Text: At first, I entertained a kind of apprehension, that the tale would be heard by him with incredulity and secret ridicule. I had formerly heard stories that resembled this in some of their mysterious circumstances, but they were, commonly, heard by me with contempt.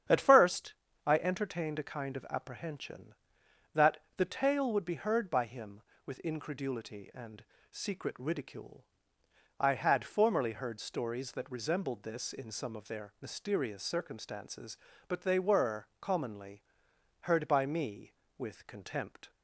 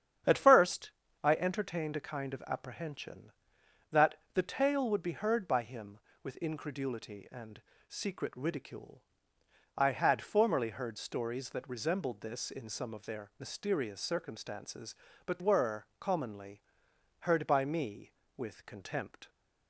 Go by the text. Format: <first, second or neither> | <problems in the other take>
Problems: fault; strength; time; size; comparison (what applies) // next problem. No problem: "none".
first | starts louder than the rest; strong; until 1.5 s; 9 dB; strong in the first // pauses between "that" and "the"; slight; at 4.1 s; 0.18 s long; slight in the first // pauses between "and" and "secret"; slight; at 7.5 s; 0.28 s long; slight in the first // skips "they"; at 15.3 s